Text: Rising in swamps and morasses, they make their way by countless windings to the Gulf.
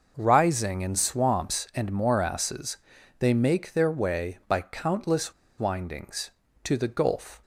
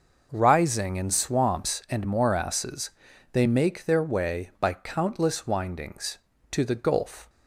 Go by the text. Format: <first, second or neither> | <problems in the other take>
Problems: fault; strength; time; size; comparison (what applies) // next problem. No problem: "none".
second | pauses between "countless" and "windings"; slight; at 5.3 s; 0.26 s long